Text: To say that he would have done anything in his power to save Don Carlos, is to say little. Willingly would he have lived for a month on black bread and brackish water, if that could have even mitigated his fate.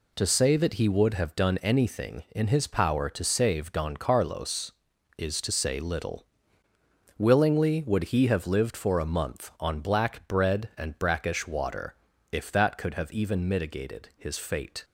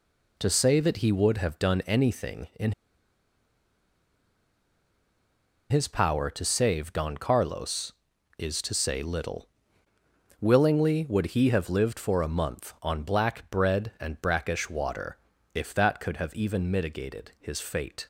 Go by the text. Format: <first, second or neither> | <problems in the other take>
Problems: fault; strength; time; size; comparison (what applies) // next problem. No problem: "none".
first | pauses between "in" and "his"; strong; at 2.7 s; 2.9 s long